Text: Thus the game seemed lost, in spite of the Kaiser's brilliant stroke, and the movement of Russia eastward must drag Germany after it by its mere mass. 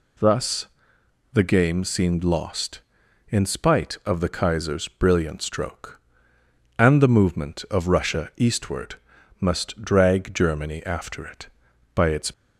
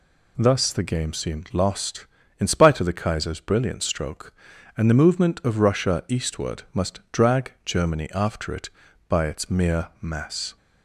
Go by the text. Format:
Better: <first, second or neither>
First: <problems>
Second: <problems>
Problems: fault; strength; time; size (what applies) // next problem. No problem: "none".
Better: second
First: pauses between "Thus" and "the"; noticeable; at 0.6 s; 0.66 s long // pauses between "eastward" and "must"; noticeable; at 8.9 s; 0.46 s long // stops before "mere mass"; at 12.3 s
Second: none